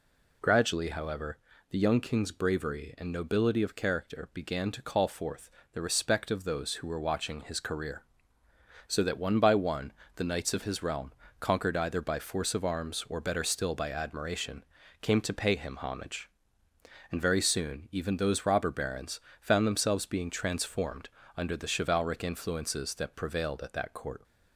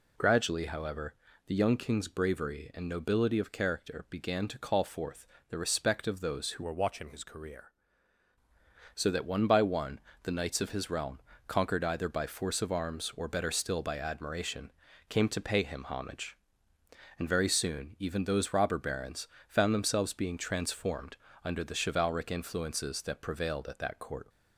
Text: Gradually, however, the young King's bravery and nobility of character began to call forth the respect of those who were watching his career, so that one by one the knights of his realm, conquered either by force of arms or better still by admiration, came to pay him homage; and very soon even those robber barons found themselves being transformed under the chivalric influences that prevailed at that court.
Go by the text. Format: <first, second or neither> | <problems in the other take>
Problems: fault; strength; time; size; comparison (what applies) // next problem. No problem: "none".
first | pauses between "forth" and "the"; slight; at 5.2 s; 0.24 s long; slight in the first // changes voice from "were" to "career"; from 6.6 to 7.7 s; 1.1 s long // pauses between "one" and "the"; slight; at 9.9 s; 0.24 s long; slight in the first // pauses between "barons" and "found"; slight; at 19.2 s; 0.22 s long; slight in the first // pauses between "transformed" and "under"; slight; at 21.1 s; 0.26 s long; slight in the first